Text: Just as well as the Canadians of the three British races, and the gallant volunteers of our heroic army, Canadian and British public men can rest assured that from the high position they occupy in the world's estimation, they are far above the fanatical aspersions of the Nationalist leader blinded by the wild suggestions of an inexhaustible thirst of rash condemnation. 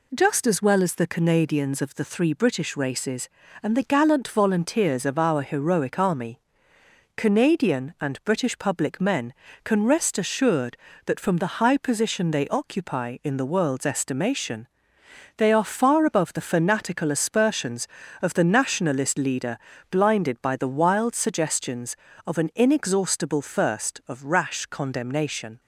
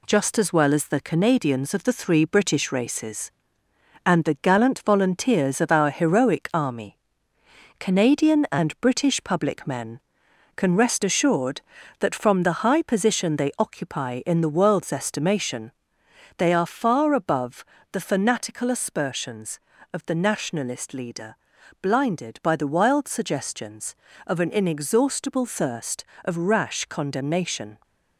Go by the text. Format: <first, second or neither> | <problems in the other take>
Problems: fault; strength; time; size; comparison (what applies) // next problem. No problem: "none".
first | gets quieter; noticeable; throughout; 4 dB // pauses between "above" and "the"; slight; at 17.6 s; 0.28 s long // pauses between "leader" and "blinded"; at 21.3 s; 0.44 s long; slight in the first